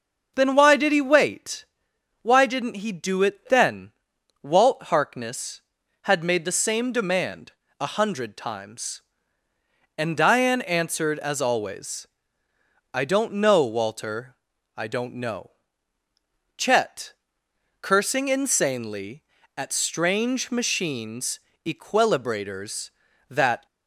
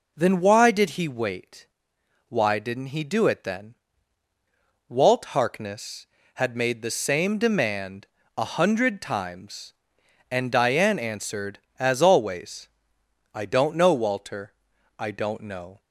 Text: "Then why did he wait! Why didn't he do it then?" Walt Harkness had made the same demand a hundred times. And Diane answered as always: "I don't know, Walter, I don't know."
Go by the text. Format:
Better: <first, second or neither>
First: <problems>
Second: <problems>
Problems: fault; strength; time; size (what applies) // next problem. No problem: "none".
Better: second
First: starts louder than the rest; noticeable; until 1.3 s; 6 dB // pauses between "demand" and "a"; slight; at 7.5 s; 0.28 s long // goes on to say "Chet cursing insanely at strange machines equilibrators that"; strong; from 16.5 s on; 7.0 s long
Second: pauses between "demand" and "a"; slight; at 8.0 s; 0.28 s long